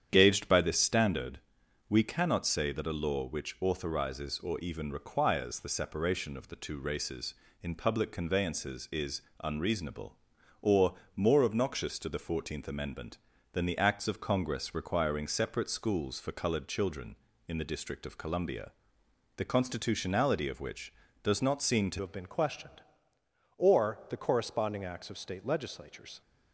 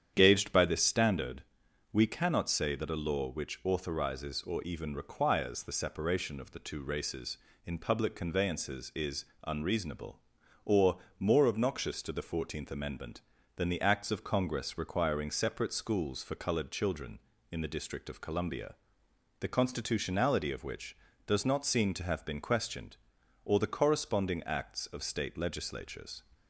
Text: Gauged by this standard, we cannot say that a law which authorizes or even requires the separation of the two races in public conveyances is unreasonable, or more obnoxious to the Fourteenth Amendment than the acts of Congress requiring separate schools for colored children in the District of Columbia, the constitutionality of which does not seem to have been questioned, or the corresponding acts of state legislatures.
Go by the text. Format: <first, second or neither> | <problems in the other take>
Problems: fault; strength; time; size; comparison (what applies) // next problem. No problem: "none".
second | starts louder than the rest; strong; until 1.1 s; 9 dB; strong in the second // pauses between "is" and "unreasonable"; slight; at 9.2 s; 0.24 s long; slight in the second // pauses between "or" and "more"; slight; at 10.9 s; 0.20 s long; slight in the second // changes voice at "have"; from 22.0 s on; 4.2 s long